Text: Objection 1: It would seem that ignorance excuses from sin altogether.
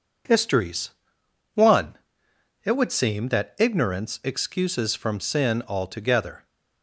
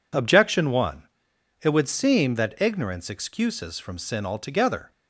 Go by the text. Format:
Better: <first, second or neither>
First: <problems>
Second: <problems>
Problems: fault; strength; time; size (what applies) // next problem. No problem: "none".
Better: second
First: says "Histories" for "Objection"; at 0.2 s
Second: none